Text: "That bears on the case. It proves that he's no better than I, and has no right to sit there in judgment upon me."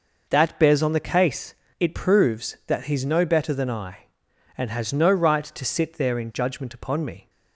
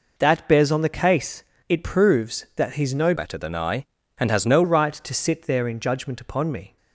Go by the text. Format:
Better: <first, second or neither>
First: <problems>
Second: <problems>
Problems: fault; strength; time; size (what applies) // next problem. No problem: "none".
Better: first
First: none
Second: changes voice from "better" to "no"; from 3.1 to 4.6 s; 1.5 s long